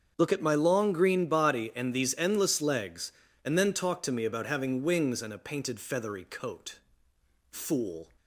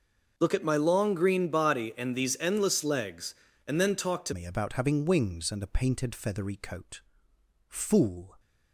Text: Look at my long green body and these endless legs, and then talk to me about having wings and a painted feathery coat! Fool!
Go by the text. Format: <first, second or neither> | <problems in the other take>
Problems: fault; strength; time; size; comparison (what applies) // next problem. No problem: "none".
first | starts louder than the rest; noticeable; until 1.3 s; 6 dB; also in the first // changes voice at "me"; from 4.3 s on; 4.0 s long